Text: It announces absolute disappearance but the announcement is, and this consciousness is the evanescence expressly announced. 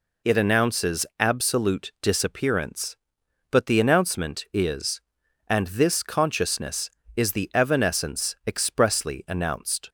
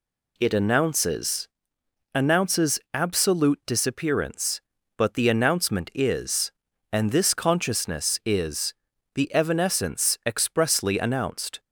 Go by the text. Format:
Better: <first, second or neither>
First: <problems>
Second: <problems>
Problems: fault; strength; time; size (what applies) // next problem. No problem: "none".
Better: first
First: none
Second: says "announces" twice; at 2.1 s // pauses between "is" and "the"; at 8.7 s; 0.40 s long